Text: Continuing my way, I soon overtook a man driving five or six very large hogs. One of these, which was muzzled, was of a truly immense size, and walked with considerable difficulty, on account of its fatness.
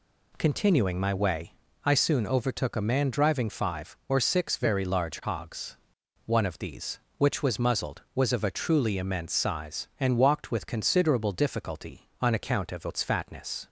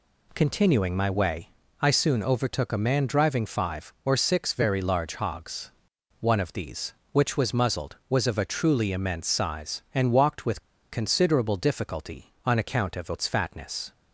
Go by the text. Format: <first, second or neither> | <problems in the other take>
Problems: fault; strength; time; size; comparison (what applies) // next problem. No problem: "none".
first | pauses between "with" and "considerable"; slight; at 10.5 s; 0.32 s long